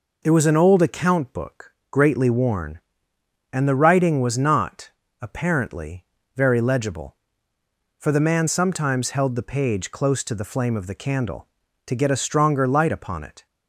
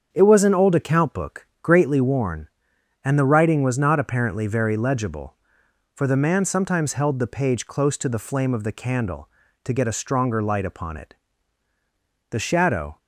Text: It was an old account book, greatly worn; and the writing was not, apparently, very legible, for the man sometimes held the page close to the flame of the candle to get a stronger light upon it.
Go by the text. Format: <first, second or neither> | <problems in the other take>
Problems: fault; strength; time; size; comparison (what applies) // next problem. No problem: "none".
first | starts louder than the rest; strong; until 1.1 s; 7.5 dB // goes on to say "The shadow"; noticeable; from 12.3 s on; 0.66 s long